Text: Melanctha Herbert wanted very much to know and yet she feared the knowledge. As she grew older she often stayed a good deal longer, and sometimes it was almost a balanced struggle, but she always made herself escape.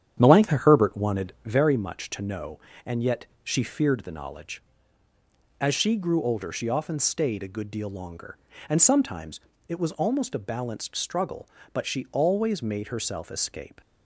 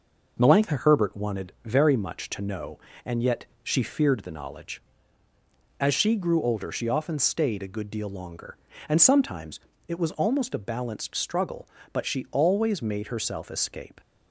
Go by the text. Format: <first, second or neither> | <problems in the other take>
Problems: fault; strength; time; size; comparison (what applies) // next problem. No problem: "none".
second | starts louder than the rest; strong; until 1.6 s; 9 dB // pauses between "yet" and "she"; slight; at 3.2 s; 0.18 s long; slight in the second // pauses between "sometimes" and "it"; slight; at 9.3 s; 0.30 s long; slight in the second